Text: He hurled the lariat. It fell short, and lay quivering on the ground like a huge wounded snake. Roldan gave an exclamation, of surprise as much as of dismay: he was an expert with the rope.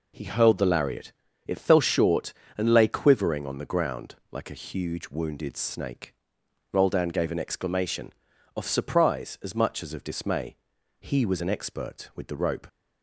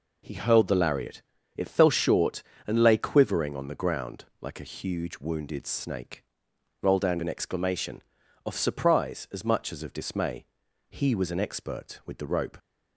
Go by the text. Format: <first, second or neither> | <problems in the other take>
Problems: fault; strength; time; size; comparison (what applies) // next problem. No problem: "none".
first | pauses between "ground" and "like"; slight; at 4.2 s; 0.16 s long; slight in the first // skips "gave"; at 7.2 s